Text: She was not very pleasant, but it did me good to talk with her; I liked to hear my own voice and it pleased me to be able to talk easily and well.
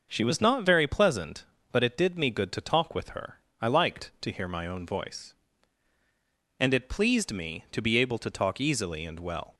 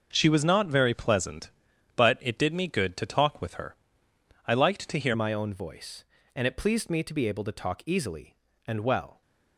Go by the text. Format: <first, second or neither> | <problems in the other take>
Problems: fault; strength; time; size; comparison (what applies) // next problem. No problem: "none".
first | starts louder than the rest; noticeable; until 1.1 s; 6 dB; noticeable in the first // changes voice at "my"; from 5.1 s on; 4.1 s long